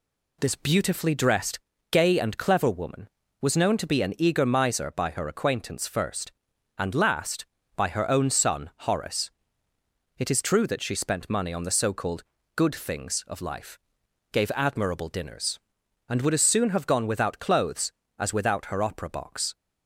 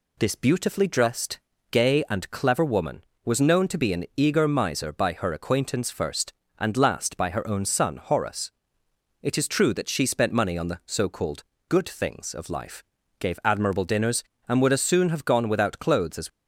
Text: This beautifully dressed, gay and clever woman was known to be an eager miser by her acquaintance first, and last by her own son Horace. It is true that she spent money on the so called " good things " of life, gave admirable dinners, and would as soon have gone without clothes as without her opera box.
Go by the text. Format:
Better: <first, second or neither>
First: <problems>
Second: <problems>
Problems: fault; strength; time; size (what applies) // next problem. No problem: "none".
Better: first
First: none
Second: stops before "without her opera box"; at 16.2 s